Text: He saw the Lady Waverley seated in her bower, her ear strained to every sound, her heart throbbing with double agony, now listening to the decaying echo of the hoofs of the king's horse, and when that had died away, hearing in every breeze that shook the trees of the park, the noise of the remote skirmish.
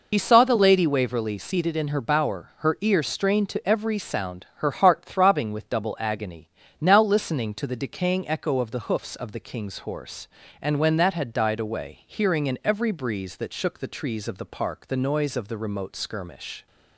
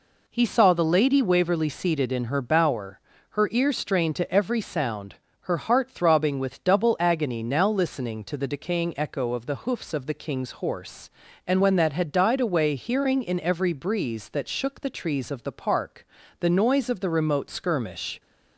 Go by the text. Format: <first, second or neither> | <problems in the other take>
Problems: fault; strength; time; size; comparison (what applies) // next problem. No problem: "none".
second | loses the start of "He"; at 0.1 s; 55 ms